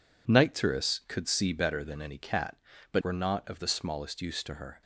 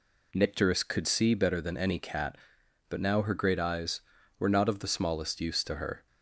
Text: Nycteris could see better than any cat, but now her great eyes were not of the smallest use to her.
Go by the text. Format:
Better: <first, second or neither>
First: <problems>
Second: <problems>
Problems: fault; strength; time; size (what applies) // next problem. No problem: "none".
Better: second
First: skips "now her great eyes"; at 3.0 s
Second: none